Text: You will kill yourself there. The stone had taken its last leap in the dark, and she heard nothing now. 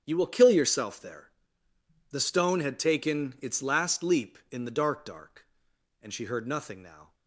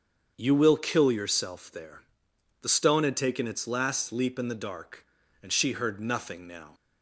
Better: second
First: starts louder than the rest; strong; until 1.0 s; 9 dB // says "dark" twice; at 5.0 s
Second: starts louder than the rest; strong; until 1.3 s; 7 dB

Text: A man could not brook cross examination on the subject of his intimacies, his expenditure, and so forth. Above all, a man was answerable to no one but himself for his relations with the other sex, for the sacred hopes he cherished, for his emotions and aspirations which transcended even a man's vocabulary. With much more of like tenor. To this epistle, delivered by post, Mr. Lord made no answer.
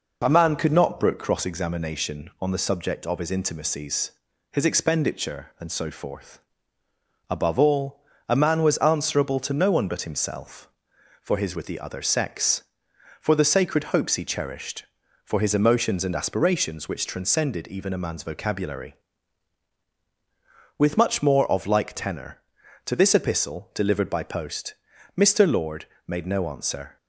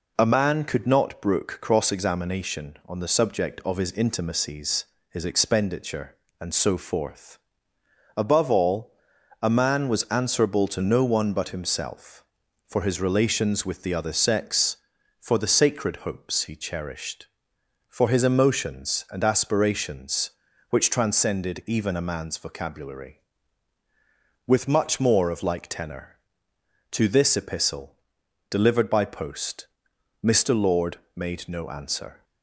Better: second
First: skips "relations"; at 11.5 s // pauses between "Lord" and "made"; slight; at 25.8 s; 0.20 s long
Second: pauses between "Lord" and "made"; slight; at 30.9 s; 0.18 s long

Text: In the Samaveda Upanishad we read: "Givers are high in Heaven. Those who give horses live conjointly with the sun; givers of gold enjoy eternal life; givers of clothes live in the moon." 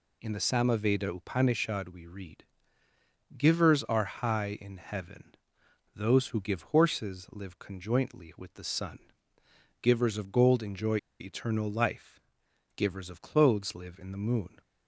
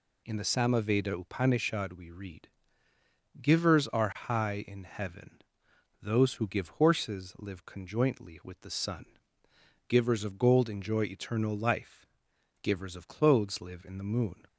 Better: second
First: pauses between "enjoy" and "eternal"; slight; at 10.9 s; 0.22 s long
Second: none

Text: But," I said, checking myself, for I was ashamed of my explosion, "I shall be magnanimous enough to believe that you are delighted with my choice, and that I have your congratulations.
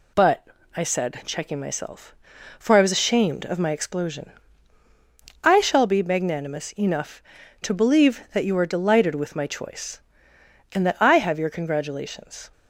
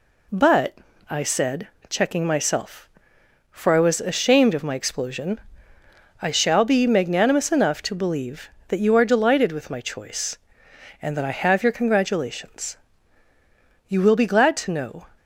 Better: first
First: none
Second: goes on to say "You will be glad to know"; noticeable; from 13.8 s on; 1.2 s long

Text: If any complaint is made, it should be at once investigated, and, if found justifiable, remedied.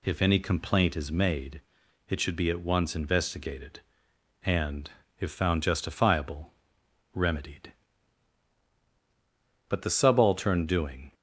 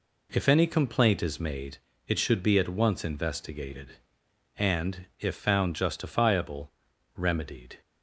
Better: second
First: goes on to say "But the subaltern doing"; from 9.6 s on; 1.4 s long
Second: none

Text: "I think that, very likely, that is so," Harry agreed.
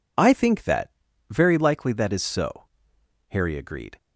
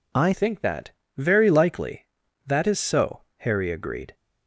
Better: first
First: none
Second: changes voice at "think"; from 0.3 s on; 3.8 s long

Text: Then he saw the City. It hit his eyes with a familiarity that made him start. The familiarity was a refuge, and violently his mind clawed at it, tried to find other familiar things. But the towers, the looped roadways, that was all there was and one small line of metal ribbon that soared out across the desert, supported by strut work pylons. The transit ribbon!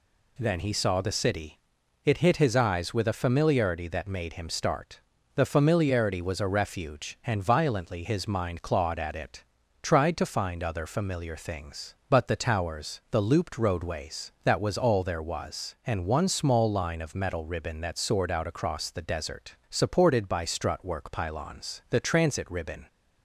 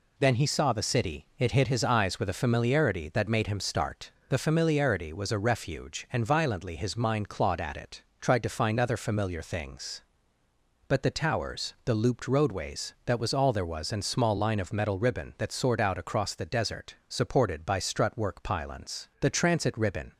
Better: first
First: none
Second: skips "one"; at 14.0 s

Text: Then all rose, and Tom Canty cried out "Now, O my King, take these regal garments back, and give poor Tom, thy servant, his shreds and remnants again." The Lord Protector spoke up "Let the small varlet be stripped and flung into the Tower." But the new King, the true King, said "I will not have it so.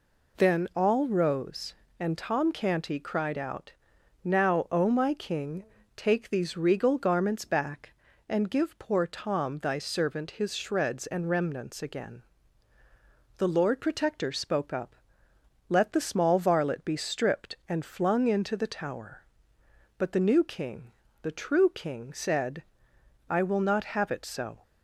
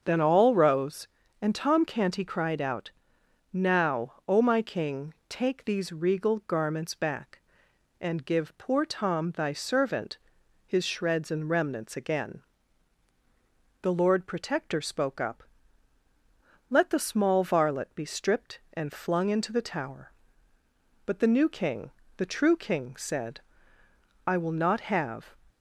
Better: first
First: pauses between "out" and "Now"; noticeable; at 3.7 s; 0.52 s long // pauses between "up" and "Let"; noticeable; at 14.9 s; 0.72 s long // pauses between "said" and "I"; noticeable; at 22.6 s; 0.68 s long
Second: starts louder than the rest; until 1.0 s; 7 dB // pauses between "out" and "Now"; noticeable; at 2.9 s; 0.60 s long // pauses between "up" and "Let"; strong; at 15.4 s; 1.2 s long // pauses between "said" and "I"; noticeable; at 23.3 s; 0.86 s long // stops before "it so"; at 25.4 s

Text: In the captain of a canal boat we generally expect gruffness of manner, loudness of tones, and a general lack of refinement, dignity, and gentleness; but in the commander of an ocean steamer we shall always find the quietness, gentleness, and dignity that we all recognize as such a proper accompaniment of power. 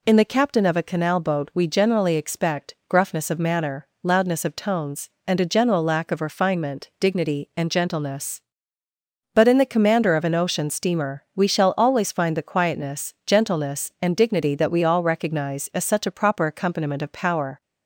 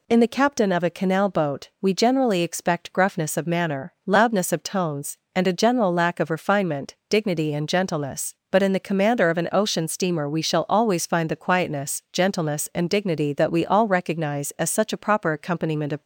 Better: first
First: none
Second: stops before "power"; at 16.0 s

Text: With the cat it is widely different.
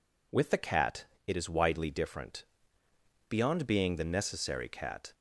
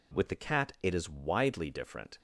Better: second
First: pauses between "cat" and "it"; slight; at 1.0 s; 0.22 s long // goes on to say "Beyond being the necessary cat"; strong; from 3.2 s on; 1.8 s long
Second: none

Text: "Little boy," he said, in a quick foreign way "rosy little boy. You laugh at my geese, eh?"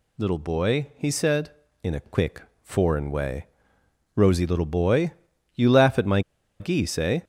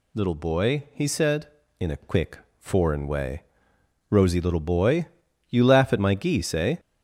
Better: second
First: pauses between "quick" and "foreign"; slight; at 2.4 s; 0.18 s long // pauses between "way" and "rosy"; noticeable; at 3.4 s; 0.68 s long // pauses between "my" and "geese"; at 6.2 s; 0.39 s long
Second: pauses between "quick" and "foreign"; slight; at 2.3 s; 0.18 s long // pauses between "way" and "rosy"; noticeable; at 3.4 s; 0.66 s long

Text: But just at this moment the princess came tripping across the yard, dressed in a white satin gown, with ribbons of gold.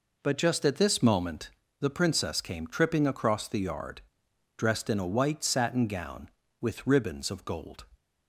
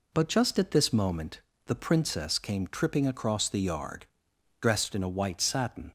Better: first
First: pauses between "moment" and "the"; slight; at 1.5 s; 0.30 s long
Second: pauses between "moment" and "the"; slight; at 1.4 s; 0.28 s long // stops before "gown with ribbons of gold"; at 5.8 s

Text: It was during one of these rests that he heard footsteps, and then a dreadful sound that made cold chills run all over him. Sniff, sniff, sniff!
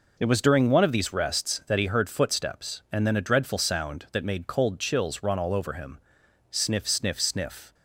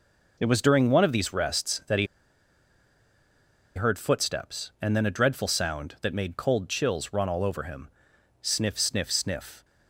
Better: first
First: none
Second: pauses between "he" and "heard"; strong; at 2.0 s; 1.7 s long

